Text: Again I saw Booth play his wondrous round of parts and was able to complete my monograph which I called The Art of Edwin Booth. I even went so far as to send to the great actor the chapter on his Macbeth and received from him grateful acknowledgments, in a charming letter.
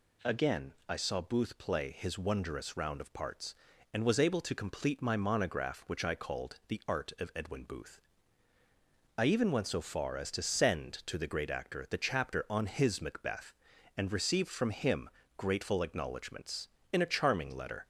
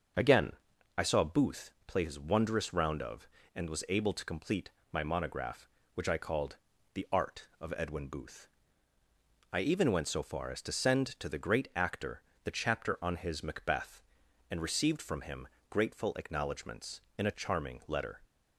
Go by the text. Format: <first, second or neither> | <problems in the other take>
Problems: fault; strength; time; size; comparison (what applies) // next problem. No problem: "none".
first | starts louder than the rest; until 1.6 s; 6 dB // pauses between "Again" and "I"; at 0.5 s; 0.44 s long // pauses between "Booth" and "play"; slight; at 1.7 s; 0.16 s long // skips "parts"; at 3.4 s // pauses between "complete" and "my"; slight; at 4.7 s; 0.22 s long // pauses between "called" and "The"; at 6.5 s; 0.38 s long // pauses between "actor" and "the"; slight; at 12.2 s; 0.22 s long // pauses between "him" and "grateful"; slight; at 15.4 s; 0.22 s long; slight in the first